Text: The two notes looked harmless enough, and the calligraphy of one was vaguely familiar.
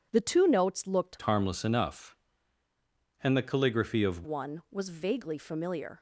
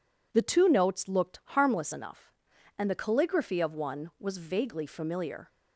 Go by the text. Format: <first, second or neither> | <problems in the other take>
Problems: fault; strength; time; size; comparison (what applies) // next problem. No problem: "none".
second | changes voice from "harmless" to "of"; from 1.2 to 4.2 s; 3.0 s long